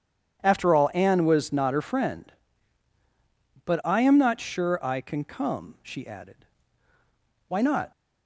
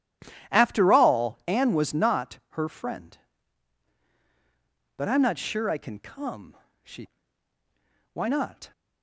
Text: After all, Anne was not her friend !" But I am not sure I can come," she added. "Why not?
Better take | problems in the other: first | starts louder than the rest; strong; until 1.6 s; 11 dB; strong in the first // skips "added"; at 7.5 s

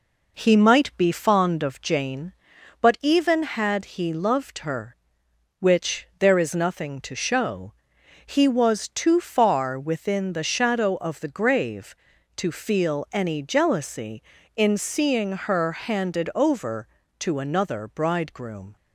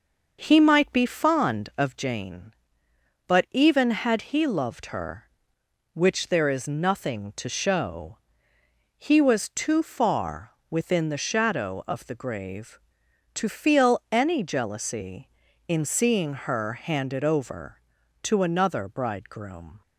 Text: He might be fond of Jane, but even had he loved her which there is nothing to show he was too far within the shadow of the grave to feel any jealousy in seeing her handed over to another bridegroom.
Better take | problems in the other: first | starts louder than the rest; until 1.8 s; 6 dB // pauses between "show" and "he"; noticeable; at 8.1 s; 0.76 s long; noticeable in the first // pauses between "far" and "within"; slight; at 10.5 s; 0.18 s long

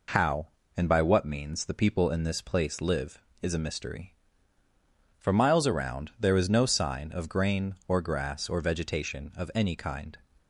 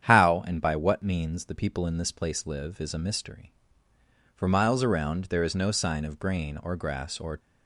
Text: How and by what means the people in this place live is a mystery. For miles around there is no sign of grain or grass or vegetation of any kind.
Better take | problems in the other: first | starts louder than the rest; strong; until 1.0 s; 9 dB // stops before "vegetation of any kind"; at 7.3 s

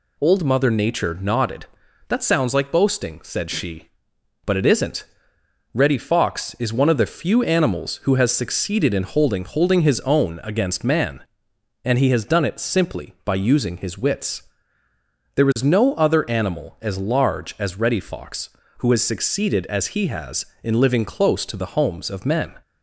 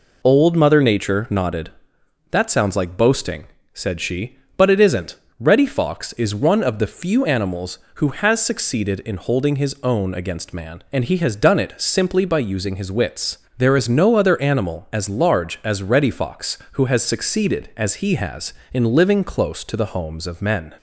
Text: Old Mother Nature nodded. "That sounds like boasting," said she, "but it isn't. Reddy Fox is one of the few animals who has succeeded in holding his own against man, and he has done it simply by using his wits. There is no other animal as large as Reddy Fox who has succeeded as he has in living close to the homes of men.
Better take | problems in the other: second | says "holding" twice; at 9.4 s

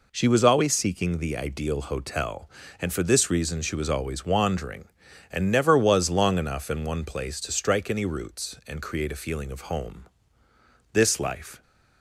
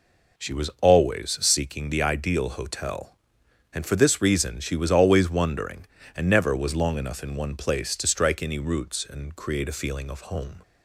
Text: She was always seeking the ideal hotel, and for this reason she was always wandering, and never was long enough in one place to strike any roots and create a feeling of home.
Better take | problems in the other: second | goes on to say "This life"; noticeable; from 10.9 s on; 0.68 s long

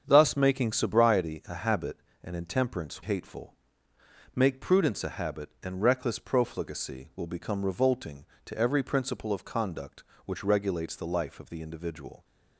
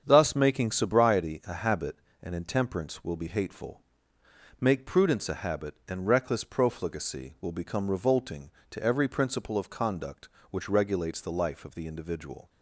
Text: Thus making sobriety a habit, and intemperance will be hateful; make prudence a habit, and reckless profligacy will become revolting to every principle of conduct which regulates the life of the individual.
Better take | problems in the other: second | starts louder than the rest; strong; until 1.0 s; 7.5 dB; strong in the second // skips "will be"; at 3.0 s

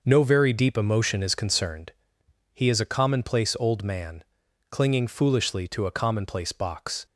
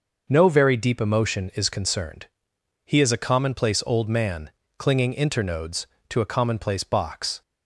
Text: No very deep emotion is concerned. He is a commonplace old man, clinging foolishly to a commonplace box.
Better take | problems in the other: first | says "internodes" for "foolishly"; at 5.1 s

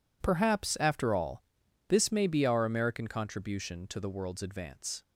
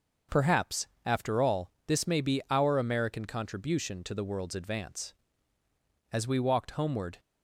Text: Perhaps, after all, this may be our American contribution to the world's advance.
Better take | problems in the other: first | starts louder than the rest; until 1.4 s; 6 dB // goes on to say "As we walked homeward"; noticeable; from 6.1 s on; 1.0 s long

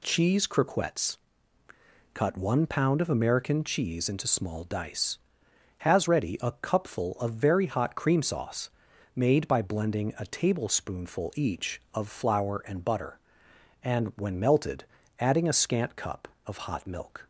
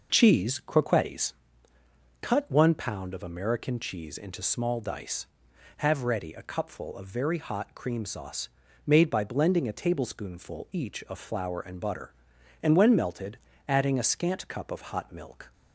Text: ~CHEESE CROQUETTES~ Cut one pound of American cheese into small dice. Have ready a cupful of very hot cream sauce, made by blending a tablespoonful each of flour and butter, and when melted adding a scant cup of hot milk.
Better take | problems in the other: second | says "Has" for "Have"; at 5.7 s // pauses between "melted" and "adding"; slight; at 14.8 s; 0.34 s long; slight in the second

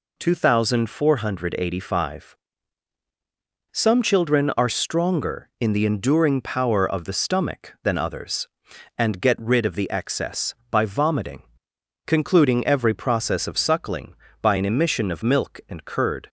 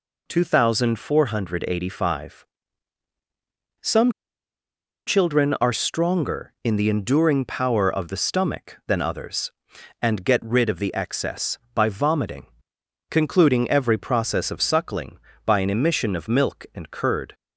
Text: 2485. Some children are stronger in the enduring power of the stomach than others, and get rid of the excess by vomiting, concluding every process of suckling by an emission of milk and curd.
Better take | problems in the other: first | pauses between "Some" and "children"; noticeable; at 4.0 s; 0.97 s long

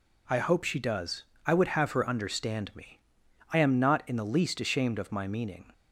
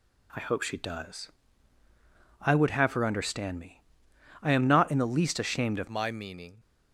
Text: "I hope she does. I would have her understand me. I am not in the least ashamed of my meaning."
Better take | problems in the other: first | changes voice at "my"; from 5.8 s on; 0.7 s long

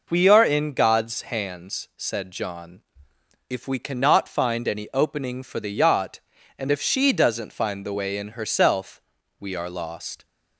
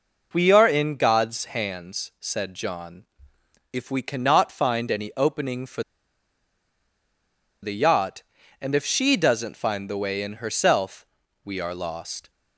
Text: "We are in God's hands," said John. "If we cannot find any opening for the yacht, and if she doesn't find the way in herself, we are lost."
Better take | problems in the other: first | pauses between "for" and "the"; strong; at 5.8 s; 1.8 s long

